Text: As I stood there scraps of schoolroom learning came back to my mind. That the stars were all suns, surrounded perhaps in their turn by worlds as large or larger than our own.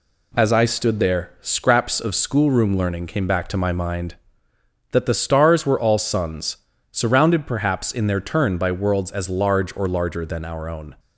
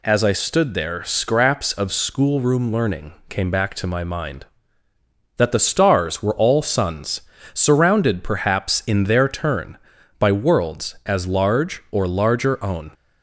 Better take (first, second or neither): first